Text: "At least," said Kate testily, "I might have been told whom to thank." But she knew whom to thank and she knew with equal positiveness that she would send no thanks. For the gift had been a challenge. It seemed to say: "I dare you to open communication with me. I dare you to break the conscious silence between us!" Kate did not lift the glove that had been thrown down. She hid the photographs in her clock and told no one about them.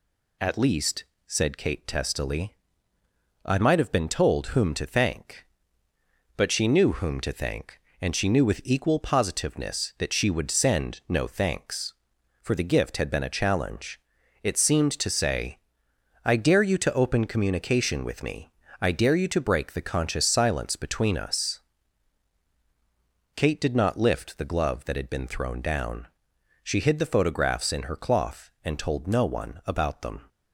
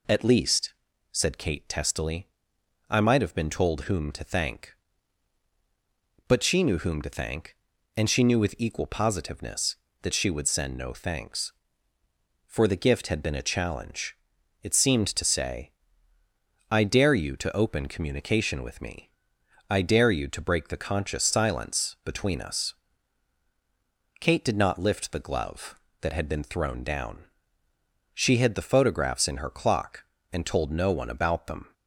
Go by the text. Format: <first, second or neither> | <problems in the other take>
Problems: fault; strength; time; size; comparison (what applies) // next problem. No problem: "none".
second | says "cloth" for "clock"; at 27.9 s